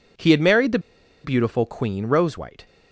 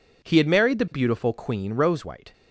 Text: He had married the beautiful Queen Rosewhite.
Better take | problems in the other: second | pauses between "the" and "beautiful"; at 0.7 s; 0.45 s long

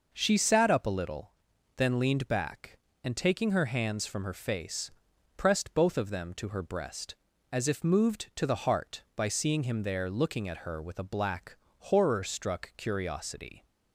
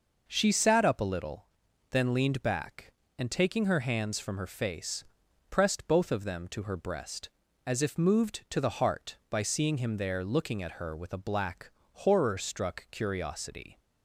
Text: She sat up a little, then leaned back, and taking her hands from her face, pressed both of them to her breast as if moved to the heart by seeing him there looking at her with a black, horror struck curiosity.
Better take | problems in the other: neither | none

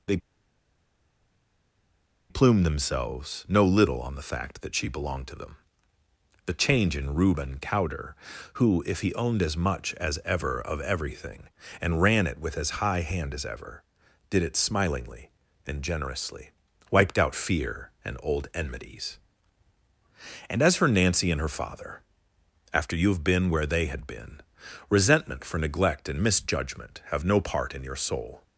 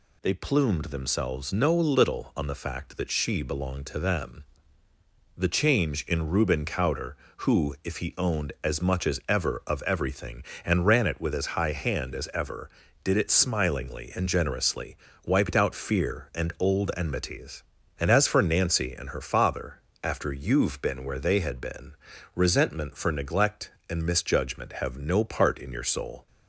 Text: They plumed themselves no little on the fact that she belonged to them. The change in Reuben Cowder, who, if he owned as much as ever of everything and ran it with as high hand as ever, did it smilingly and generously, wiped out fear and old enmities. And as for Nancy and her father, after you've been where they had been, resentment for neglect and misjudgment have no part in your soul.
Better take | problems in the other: second | pauses between "They" and "plumed"; strong; at 0.1 s; 2.1 s long

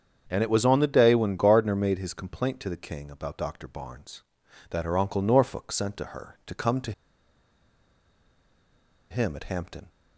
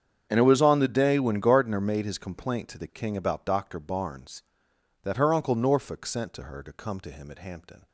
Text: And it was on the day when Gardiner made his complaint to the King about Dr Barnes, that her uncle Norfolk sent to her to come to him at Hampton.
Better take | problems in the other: second | starts louder than the rest; strong; until 1.3 s; 7.5 dB; strong in the second // pauses between "to" and "him"; strong; at 6.9 s; 2.1 s long

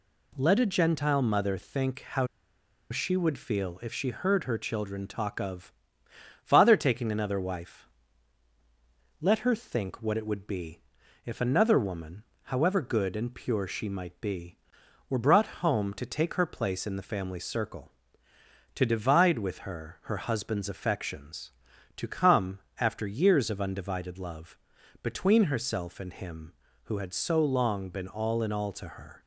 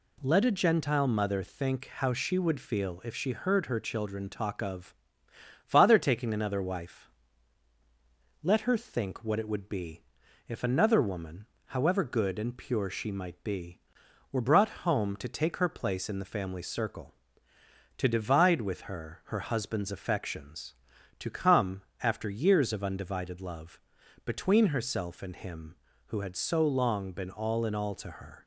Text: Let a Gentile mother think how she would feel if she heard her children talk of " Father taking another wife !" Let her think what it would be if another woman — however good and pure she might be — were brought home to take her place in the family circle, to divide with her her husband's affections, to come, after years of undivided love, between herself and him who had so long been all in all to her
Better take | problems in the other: second | pauses between "how" and "she"; noticeable; at 2.2 s; 0.64 s long // pauses between "be" and "if"; at 10.7 s; 0.44 s long; also in the second

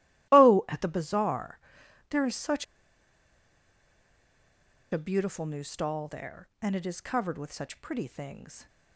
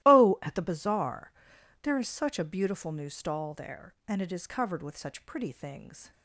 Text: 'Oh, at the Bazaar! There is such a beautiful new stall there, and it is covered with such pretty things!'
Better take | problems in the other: second | starts louder than the rest; strong; until 1.3 s; 15.5 dB; strong in the second // pauses between "such" and "a"; strong; at 2.6 s; 2.2 s long

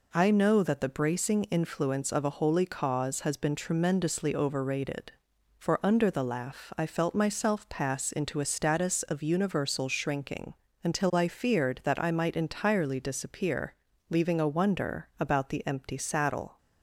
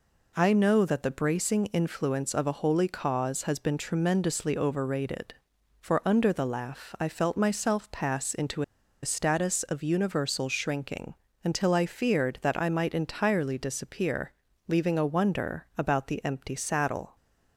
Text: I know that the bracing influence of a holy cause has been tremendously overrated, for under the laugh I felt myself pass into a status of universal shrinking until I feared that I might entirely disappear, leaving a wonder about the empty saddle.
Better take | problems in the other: first | pauses between "into" and "a"; at 8.6 s; 0.39 s long // pauses between "shrinking" and "until"; slight; at 11.1 s; 0.28 s long; slight in the first

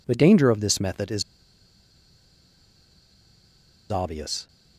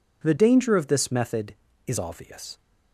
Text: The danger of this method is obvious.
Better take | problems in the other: second | pauses between "is" and "obvious"; strong; at 1.2 s; 2.6 s long

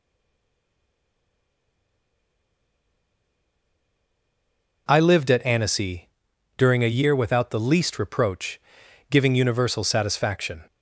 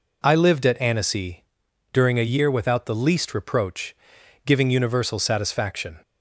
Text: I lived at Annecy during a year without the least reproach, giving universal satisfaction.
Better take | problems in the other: second | stays silent before the first word; strong; until 4.8 s; 4.8 s long // pauses between "Annecy" and "during"; noticeable; at 6.0 s; 0.50 s long; noticeable in the second

